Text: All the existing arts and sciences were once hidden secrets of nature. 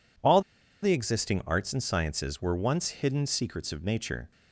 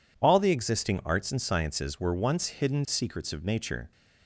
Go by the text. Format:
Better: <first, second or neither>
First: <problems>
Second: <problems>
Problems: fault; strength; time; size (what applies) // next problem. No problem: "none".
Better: second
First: pauses between "All" and "the"; at 0.4 s; 0.41 s long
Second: none